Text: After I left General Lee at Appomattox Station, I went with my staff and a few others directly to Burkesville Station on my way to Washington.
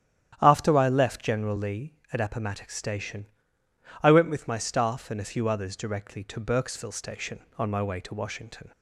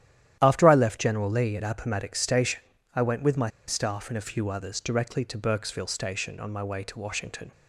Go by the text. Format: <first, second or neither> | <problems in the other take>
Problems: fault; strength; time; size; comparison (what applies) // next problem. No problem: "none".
first | starts louder than the rest; strong; until 1.4 s; 11.5 dB; strong in the first // pauses between "my" and "staff"; slight; at 3.4 s; 0.17 s long